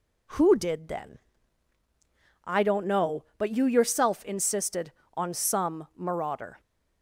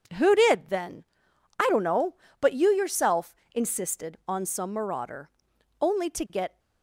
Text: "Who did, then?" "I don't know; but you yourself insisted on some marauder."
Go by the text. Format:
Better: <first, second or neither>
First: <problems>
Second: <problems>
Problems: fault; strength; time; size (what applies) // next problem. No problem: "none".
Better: first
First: none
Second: pauses between "yourself" and "insisted"; slight; at 3.3 s; 0.22 s long // goes on to say "Only to get"; noticeable; from 5.8 s on; 0.76 s long